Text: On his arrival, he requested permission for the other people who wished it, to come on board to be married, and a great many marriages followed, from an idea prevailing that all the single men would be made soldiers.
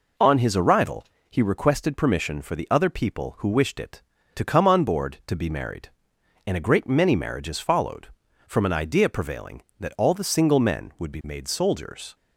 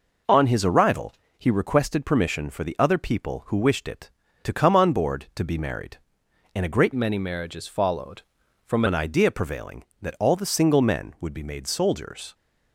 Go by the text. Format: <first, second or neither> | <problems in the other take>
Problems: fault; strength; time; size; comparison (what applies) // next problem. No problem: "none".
first | changes voice from "many" to "from"; from 6.9 to 8.8 s; 1.9 s long